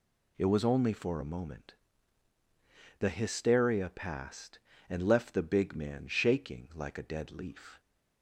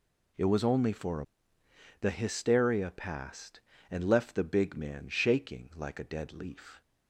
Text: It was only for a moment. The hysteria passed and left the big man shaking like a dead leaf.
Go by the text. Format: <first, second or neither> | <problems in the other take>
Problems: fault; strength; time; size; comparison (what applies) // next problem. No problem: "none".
first | skips "moment"; at 1.6 s